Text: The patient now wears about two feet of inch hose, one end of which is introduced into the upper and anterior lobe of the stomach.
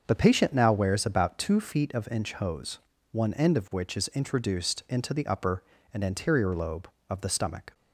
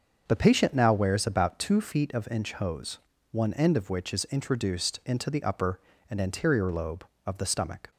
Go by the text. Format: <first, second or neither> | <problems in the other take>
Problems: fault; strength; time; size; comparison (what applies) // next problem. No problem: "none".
neither | starts louder than the rest; the same in both